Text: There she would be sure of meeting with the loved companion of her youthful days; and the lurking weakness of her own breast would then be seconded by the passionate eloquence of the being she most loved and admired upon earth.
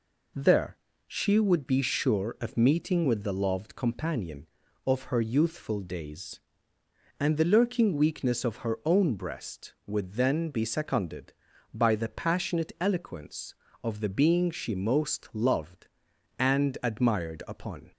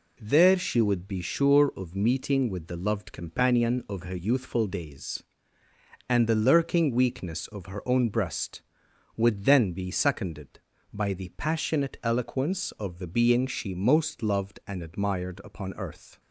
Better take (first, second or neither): second